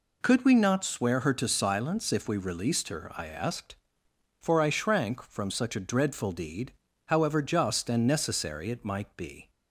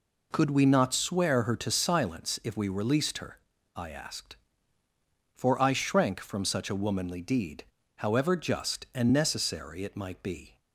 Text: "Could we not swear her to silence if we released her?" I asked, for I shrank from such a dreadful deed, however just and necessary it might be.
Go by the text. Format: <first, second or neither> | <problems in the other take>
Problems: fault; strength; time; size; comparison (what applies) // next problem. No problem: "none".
first | says "womanly" for "dreadful"; at 6.7 s